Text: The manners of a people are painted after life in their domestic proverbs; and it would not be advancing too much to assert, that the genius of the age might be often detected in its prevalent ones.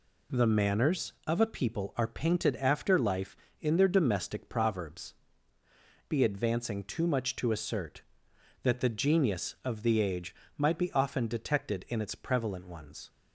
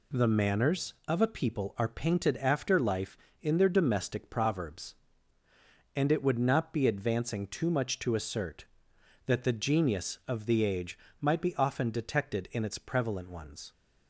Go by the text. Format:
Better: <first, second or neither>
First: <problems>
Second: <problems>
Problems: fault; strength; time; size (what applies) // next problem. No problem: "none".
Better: second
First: skips "and it would not"; at 5.6 s // pauses between "age" and "might"; slight; at 10.3 s; 0.24 s long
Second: pauses between "age" and "might"; slight; at 10.9 s; 0.24 s long